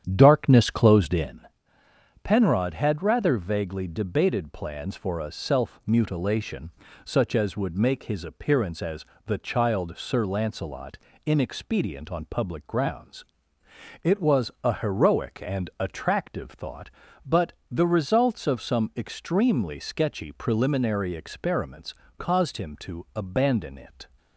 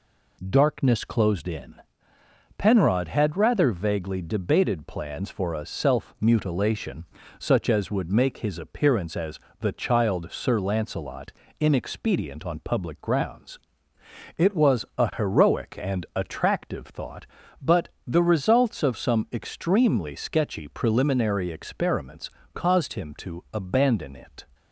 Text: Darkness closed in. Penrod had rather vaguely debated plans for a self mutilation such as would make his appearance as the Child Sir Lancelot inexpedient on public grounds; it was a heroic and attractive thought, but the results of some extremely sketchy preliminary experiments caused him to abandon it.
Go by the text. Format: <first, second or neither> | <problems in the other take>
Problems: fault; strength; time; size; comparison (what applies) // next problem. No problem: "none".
second | starts louder than the rest; strong; until 1.3 s; 9 dB // pauses between "mutilation" and "such"; slight; at 6.7 s; 0.34 s long; slight in the second // pauses between "as" and "the"; slight; at 9.0 s; 0.22 s long; slight in the second // pauses between "Lancelot" and "inexpedient"; slight; at 10.9 s; 0.28 s long; slight in the second // pauses between "but" and "the"; slight; at 17.5 s; 0.16 s long; slight in the second // pauses between "experiments" and "caused"; slight; at 21.9 s; 0.24 s long; slight in the second